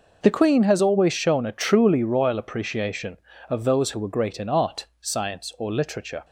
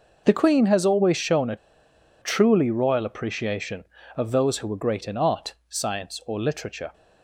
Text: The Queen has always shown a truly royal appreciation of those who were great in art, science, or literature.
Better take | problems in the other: first | pauses between "a" and "truly"; noticeable; at 1.5 s; 0.65 s long

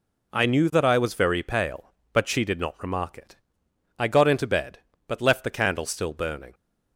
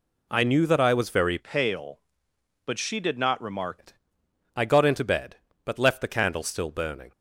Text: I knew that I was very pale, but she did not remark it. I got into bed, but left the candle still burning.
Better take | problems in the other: first | changes voice from "pale" to "remark"; from 1.3 to 3.7 s; 2.4 s long

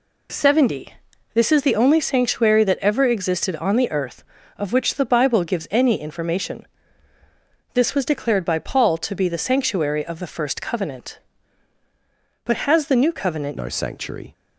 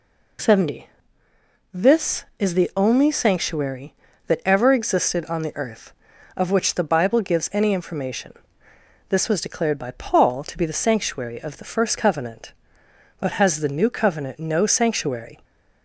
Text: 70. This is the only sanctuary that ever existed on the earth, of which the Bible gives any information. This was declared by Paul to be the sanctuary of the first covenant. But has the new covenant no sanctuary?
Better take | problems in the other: second | changes voice at "no"; from 13.5 s on; 0.8 s long

